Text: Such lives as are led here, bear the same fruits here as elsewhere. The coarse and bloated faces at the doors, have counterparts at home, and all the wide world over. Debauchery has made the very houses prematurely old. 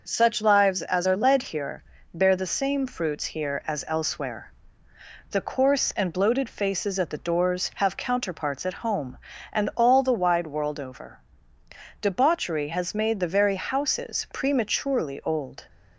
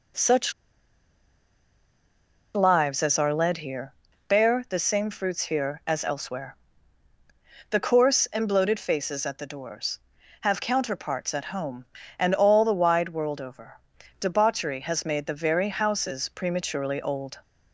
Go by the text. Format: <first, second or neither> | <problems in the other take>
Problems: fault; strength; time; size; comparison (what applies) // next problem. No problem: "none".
first | pauses between "Such" and "lives"; strong; at 0.5 s; 2.0 s long